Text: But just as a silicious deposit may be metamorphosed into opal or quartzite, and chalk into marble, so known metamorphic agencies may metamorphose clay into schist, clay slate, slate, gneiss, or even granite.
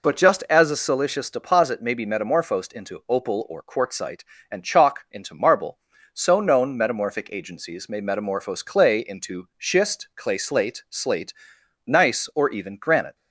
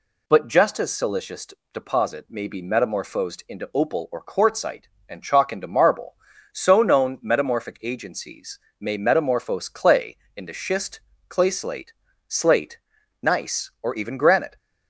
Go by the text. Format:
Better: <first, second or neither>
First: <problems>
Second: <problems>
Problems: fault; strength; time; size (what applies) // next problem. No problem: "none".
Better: first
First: none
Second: skips "a"; at 0.9 s // pauses between "silicious" and "deposit"; slight; at 1.4 s; 0.26 s long // pauses between "agencies" and "may"; slight; at 8.5 s; 0.22 s long // pauses between "clay" and "into"; slight; at 10.1 s; 0.20 s long